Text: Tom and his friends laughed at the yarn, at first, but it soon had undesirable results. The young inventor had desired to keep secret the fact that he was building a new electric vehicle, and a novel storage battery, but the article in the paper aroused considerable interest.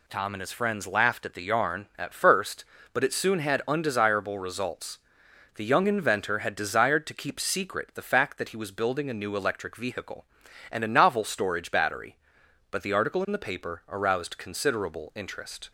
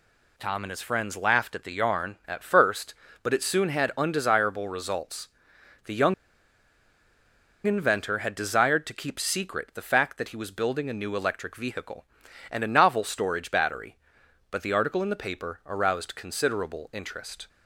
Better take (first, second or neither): first